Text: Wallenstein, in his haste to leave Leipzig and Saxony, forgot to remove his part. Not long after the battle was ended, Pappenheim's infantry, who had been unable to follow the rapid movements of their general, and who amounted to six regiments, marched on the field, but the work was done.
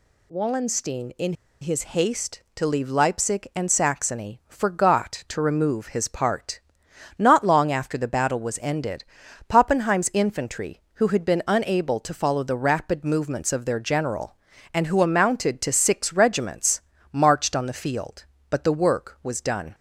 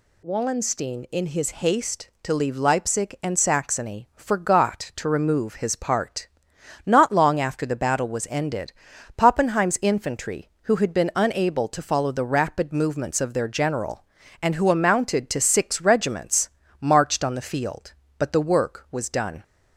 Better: second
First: pauses between "in" and "his"; slight; at 1.3 s; 0.28 s long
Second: none

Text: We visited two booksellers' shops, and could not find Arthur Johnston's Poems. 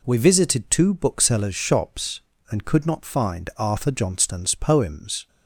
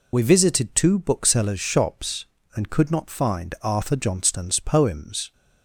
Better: first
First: none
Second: loses the start of "We"; at 0.1 s; 40 ms

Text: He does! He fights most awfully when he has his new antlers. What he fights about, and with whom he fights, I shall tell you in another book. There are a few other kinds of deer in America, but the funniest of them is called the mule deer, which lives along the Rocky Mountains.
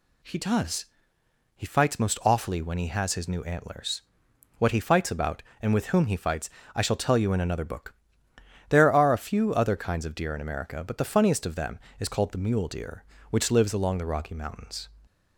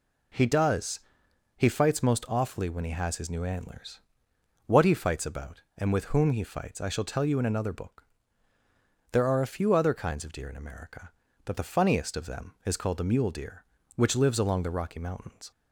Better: neither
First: none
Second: none

